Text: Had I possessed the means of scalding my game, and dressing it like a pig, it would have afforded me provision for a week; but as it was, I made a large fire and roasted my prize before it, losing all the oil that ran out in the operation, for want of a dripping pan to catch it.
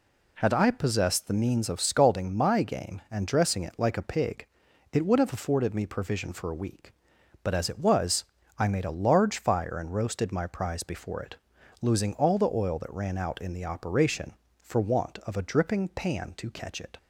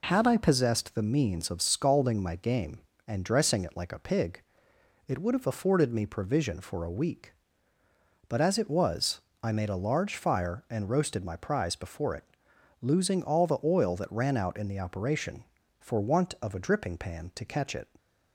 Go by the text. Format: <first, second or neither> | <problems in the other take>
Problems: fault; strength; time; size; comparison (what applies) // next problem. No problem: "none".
neither | none